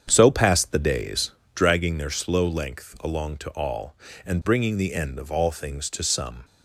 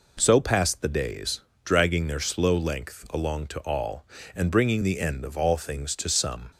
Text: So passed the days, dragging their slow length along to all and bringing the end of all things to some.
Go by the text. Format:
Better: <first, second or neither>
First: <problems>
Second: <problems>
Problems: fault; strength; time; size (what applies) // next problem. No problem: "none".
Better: second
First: starts louder than the rest; strong; until 1.7 s; 8 dB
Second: none